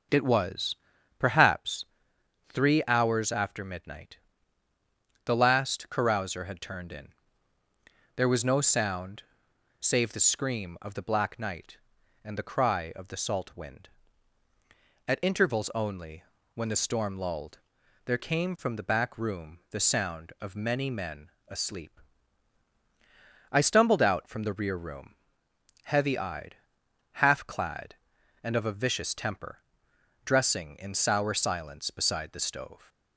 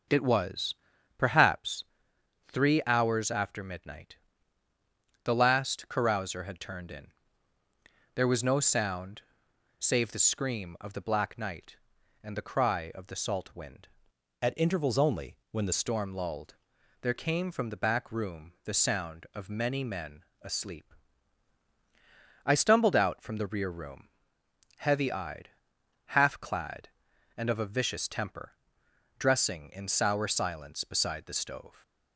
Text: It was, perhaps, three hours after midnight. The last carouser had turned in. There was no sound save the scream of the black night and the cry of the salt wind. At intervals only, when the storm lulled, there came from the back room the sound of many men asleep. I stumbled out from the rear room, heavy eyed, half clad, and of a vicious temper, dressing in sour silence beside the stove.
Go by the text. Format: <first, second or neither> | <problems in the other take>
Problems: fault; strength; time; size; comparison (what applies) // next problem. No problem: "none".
first | starts louder than the rest; until 1.5 s; 6.5 dB; also in the first // pauses between "sound" and "save"; noticeable; at 9.2 s; 0.58 s long; noticeable in the first // changes voice from "At" to "the"; from 14.4 to 15.7 s; 1.3 s long // pauses between "men" and "asleep"; slight; at 20.2 s; 0.18 s long; slight in the first